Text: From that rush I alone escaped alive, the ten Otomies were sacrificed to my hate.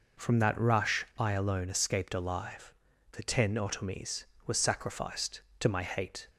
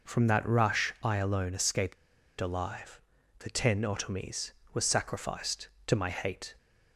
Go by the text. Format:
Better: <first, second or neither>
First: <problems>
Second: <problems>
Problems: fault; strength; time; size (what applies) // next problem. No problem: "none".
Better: first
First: none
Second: pauses between "escaped" and "alive"; at 1.9 s; 0.44 s long